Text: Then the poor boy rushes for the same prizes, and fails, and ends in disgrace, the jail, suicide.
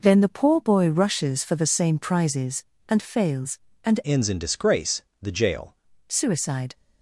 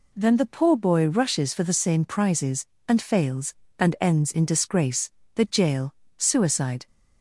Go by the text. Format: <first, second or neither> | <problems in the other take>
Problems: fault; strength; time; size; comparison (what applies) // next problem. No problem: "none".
second | changes voice from "ends" to "jail"; from 4.0 to 5.7 s; 1.7 s long